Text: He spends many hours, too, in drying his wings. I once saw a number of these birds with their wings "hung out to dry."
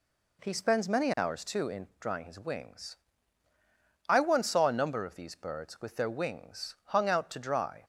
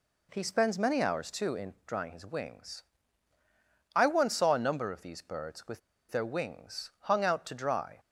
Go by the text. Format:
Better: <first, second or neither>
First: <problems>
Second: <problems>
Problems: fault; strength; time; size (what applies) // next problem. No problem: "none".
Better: first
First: none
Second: pauses between "with" and "their"; slight; at 5.7 s; 0.29 s long